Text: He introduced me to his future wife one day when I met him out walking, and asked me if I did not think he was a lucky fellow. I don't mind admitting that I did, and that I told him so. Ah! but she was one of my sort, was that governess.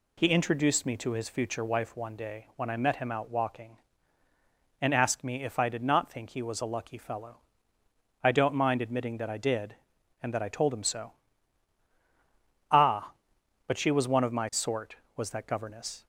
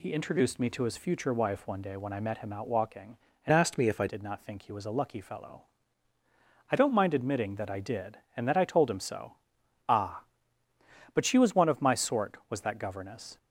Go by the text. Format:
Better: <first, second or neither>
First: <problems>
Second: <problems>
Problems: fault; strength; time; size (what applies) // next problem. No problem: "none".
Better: first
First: none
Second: changes voice from "asked" to "I"; from 3.5 to 4.0 s; 0.5 s long